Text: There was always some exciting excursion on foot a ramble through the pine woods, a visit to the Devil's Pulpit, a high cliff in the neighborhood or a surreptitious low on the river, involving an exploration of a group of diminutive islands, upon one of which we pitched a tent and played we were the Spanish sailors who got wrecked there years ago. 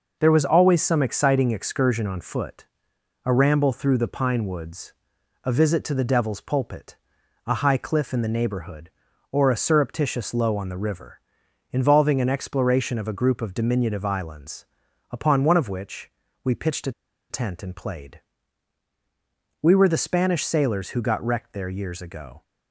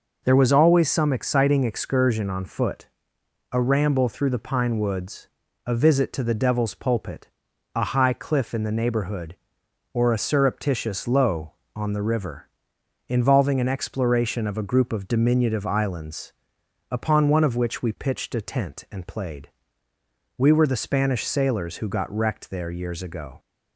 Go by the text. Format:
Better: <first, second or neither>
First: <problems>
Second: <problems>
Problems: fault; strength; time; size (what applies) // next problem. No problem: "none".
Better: second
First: pauses between "foot" and "a"; noticeable; at 2.6 s; 0.60 s long // pauses between "which" and "we"; slight; at 16.0 s; 0.34 s long // pauses between "a" and "tent"; at 16.9 s; 0.38 s long // pauses between "played" and "we"; strong; at 18.2 s; 1.4 s long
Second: pauses between "foot" and "a"; noticeable; at 2.8 s; 0.66 s long // pauses between "played" and "we"; noticeable; at 19.4 s; 0.88 s long